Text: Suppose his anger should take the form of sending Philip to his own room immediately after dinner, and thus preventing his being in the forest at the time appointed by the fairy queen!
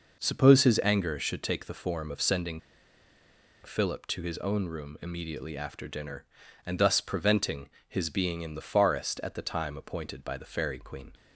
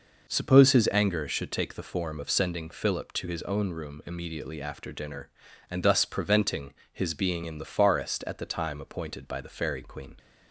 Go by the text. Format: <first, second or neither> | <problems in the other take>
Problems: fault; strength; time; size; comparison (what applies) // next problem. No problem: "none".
second | pauses between "sending" and "Philip"; at 2.5 s; 1.0 s long // pauses between "preventing" and "his"; slight; at 7.6 s; 0.20 s long; slight in the second